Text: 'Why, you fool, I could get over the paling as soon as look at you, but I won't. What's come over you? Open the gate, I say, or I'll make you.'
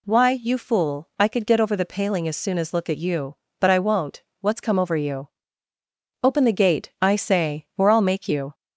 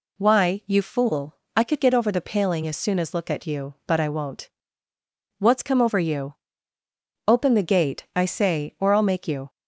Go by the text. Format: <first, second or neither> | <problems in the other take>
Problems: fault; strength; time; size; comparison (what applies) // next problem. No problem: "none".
neither | none